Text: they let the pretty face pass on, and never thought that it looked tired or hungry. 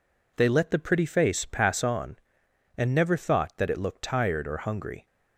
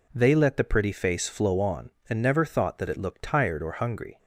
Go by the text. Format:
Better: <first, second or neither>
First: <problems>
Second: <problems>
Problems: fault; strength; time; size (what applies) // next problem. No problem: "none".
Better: first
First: none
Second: says "flow" for "pass"; at 1.2 s